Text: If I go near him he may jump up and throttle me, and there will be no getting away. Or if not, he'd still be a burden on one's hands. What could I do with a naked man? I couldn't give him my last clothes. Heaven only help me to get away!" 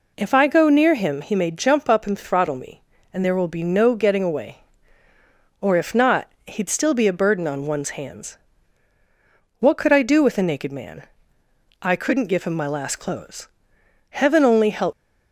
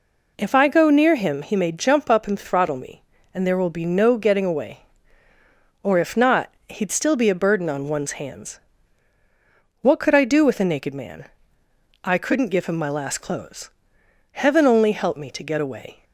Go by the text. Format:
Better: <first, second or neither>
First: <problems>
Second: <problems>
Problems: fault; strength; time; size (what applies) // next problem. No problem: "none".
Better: second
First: stops before "me to get away"; at 14.9 s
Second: none